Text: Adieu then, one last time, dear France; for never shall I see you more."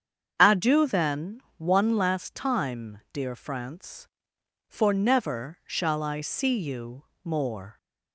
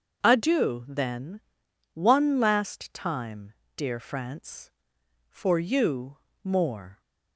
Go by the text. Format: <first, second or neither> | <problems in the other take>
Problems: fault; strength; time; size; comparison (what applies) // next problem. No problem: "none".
first | starts louder than the rest; until 1.2 s; 6.5 dB; strong in the first // skips "never shall I see"; at 5.5 s // pauses between "you" and "more"; slight; at 6.1 s; 0.26 s long; slight in the first